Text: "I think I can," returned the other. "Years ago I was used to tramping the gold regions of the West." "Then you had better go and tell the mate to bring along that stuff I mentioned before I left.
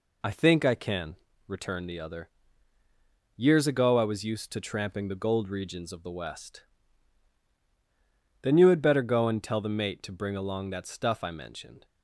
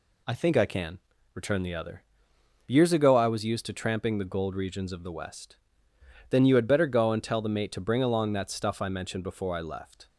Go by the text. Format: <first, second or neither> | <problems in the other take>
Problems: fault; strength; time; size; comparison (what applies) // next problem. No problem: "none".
second | stops before "before I left"; at 11.8 s